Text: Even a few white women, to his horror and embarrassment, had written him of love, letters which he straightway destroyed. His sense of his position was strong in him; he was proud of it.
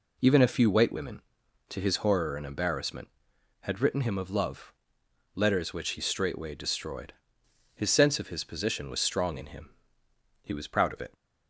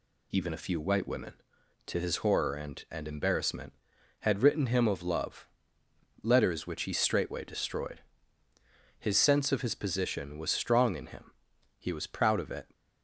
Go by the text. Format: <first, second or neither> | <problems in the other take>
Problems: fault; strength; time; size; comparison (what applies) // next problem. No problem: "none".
first | says "and" twice; at 2.9 s